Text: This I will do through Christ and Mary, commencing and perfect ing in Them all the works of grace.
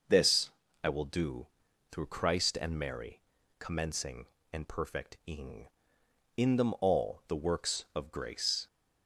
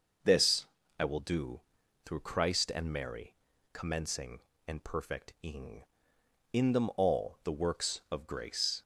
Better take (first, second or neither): neither